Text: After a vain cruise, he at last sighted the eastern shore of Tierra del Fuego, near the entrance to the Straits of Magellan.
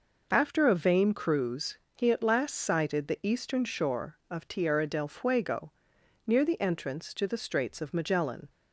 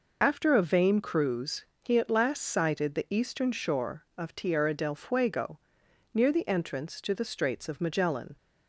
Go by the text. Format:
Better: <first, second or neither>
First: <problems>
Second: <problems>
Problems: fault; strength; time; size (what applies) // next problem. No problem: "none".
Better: first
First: none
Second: loses the start of "After"; at 0.2 s; 35 ms